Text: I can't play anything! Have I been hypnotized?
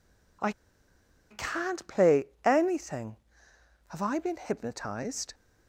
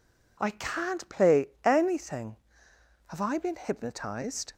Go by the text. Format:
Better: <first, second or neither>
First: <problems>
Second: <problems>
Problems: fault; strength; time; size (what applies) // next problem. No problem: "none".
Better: second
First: pauses between "I" and "can't"; noticeable; at 0.5 s; 0.77 s long // pauses between "play" and "anything"; slight; at 2.2 s; 0.18 s long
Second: pauses between "play" and "anything"; slight; at 1.4 s; 0.16 s long